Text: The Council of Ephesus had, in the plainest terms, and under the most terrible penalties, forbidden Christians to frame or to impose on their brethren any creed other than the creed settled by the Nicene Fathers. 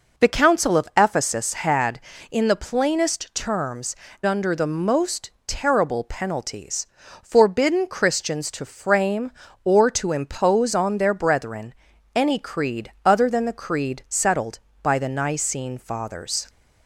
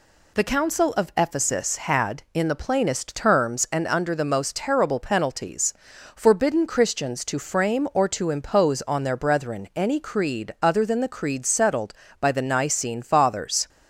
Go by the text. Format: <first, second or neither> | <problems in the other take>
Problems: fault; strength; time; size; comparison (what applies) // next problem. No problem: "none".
second | skips "and"; at 4.1 s // pauses between "most" and "terrible"; slight; at 5.3 s; 0.16 s long // pauses between "brethren" and "any"; at 11.7 s; 0.42 s long